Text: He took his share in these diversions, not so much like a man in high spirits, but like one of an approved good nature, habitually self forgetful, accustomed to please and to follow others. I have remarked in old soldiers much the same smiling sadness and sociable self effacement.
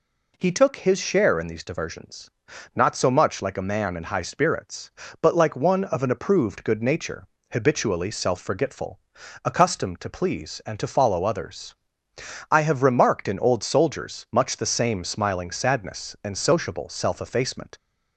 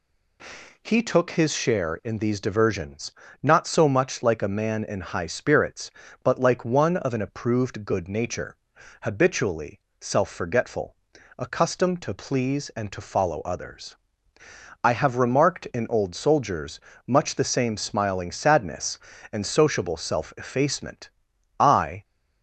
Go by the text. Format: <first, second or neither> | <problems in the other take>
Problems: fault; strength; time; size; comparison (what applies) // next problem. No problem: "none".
first | pauses between "habitually" and "self"; slight; at 9.7 s; 0.22 s long // pauses between "soldiers" and "much"; slight; at 16.7 s; 0.28 s long // goes on to say "I"; slight; from 21.5 s on; 0.46 s long